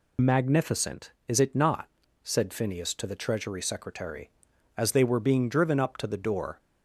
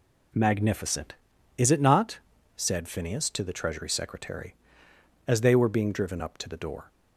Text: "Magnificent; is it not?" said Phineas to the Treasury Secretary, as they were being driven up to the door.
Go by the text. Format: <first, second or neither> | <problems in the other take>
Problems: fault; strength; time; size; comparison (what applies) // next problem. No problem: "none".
second | loses the start of "Magnificent"; at 0.1 s; 25 ms